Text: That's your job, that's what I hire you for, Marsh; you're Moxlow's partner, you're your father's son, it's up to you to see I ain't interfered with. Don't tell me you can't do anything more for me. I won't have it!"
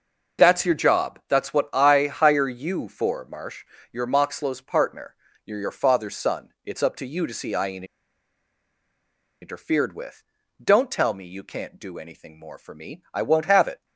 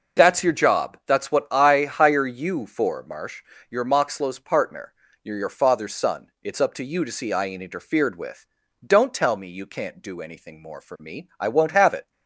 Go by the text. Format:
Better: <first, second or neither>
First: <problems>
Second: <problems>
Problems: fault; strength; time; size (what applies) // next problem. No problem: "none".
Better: second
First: pauses between "ain't" and "interfered"; strong; at 7.8 s; 1.5 s long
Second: none